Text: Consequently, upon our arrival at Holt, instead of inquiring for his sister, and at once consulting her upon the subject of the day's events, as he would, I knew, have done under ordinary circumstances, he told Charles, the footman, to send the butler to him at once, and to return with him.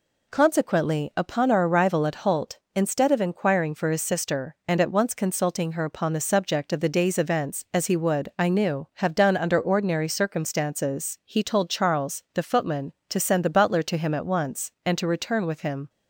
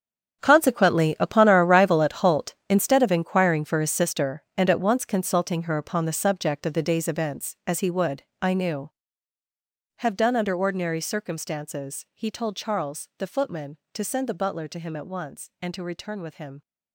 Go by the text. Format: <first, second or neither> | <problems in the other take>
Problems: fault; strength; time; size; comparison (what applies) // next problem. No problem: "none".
first | gets quieter; strong; throughout; 14 dB